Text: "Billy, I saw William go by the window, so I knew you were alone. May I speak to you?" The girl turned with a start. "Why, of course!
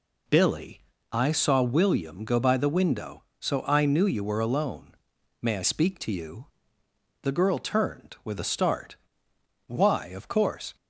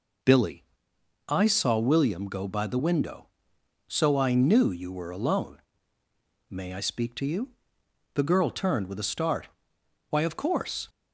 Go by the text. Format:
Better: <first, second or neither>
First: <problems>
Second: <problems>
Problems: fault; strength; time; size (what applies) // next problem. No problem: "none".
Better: neither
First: none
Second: none